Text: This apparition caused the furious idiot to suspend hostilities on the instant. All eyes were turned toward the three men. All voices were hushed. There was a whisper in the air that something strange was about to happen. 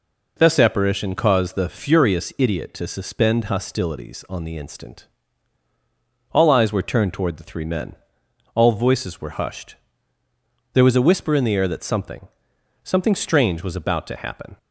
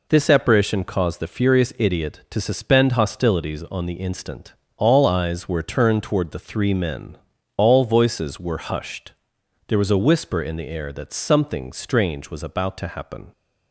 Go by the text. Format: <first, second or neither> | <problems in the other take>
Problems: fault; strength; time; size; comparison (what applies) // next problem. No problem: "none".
second | says "something" twice; at 12.8 s